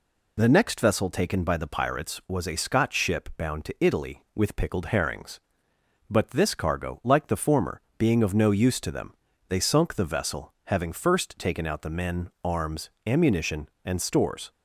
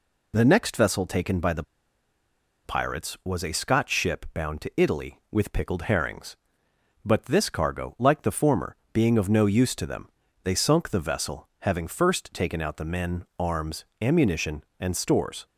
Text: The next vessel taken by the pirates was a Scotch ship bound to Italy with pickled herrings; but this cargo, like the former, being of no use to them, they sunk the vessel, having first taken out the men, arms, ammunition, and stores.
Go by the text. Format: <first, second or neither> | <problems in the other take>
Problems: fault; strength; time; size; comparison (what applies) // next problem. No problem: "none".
first | pauses between "the" and "pirates"; at 1.6 s; 1.0 s long